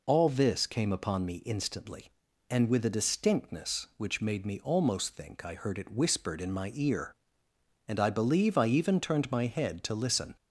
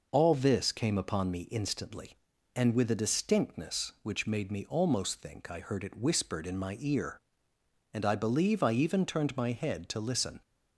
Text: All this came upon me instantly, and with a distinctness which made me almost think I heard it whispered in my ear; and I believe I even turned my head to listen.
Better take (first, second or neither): first